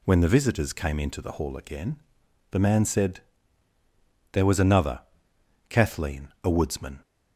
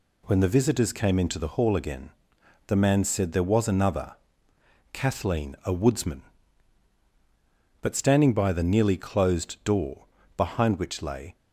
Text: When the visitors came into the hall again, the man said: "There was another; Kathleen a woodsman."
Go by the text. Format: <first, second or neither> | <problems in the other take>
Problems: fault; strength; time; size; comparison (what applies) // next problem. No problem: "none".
first | goes on to say "But standing by the nearly closed door behind which lay"; strong; from 7.8 s on; 3.5 s long